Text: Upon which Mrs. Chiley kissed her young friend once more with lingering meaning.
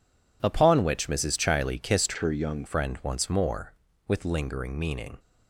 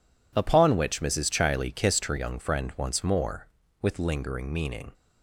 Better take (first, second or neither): second